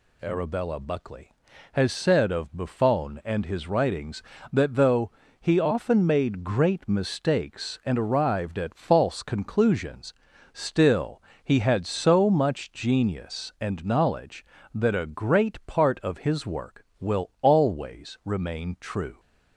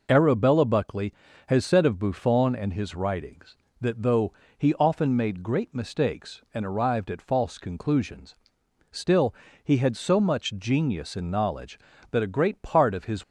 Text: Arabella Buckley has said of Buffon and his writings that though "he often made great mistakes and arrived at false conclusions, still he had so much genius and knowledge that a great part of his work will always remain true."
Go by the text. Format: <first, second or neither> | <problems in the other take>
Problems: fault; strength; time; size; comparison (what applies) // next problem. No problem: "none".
first | pauses between "though" and "he"; slight; at 4.3 s; 0.26 s long; slight in the first // pauses between "still" and "he"; slight; at 9.3 s; 0.30 s long; slight in the first // stops before "work will always remain true"; at 13.2 s